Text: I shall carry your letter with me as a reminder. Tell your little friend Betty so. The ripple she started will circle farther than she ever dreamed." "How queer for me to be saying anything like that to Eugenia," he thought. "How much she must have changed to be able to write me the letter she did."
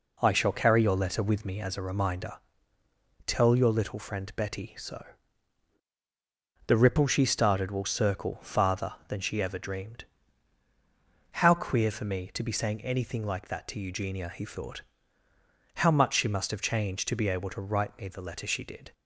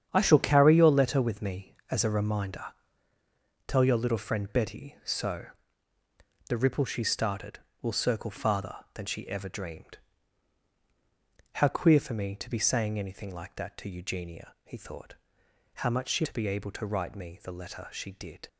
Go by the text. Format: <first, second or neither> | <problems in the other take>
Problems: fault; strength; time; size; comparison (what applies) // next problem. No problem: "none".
first | starts louder than the rest; strong; until 1.1 s; 8.5 dB // skips "must have changed"; at 16.2 s